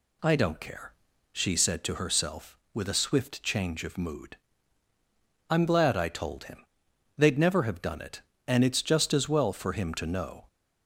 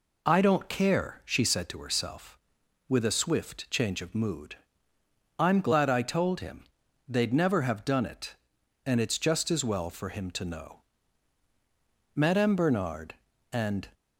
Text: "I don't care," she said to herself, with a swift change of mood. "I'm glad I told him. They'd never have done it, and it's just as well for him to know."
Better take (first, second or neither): first